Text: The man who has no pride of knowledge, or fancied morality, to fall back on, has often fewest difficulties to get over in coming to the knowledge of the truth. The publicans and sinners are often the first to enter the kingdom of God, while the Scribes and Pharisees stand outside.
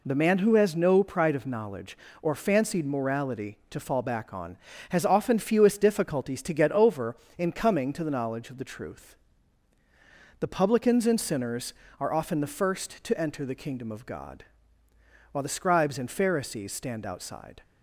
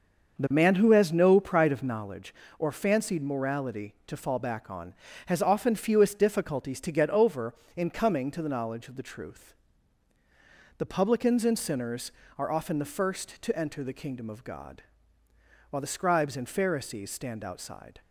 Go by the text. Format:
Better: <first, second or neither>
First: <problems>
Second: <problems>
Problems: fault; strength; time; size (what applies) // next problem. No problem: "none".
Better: first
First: none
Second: starts louder than the rest; until 2.1 s; 6.5 dB